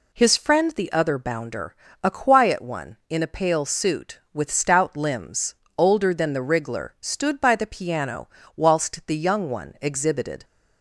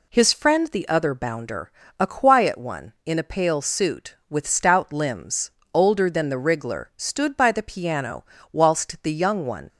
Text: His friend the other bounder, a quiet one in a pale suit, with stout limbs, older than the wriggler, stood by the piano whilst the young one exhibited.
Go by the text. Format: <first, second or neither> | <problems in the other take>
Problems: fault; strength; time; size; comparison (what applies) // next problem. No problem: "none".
first | pauses between "piano" and "whilst"; slight; at 8.2 s; 0.26 s long; slight in the first // stops before "exhibited"; at 9.6 s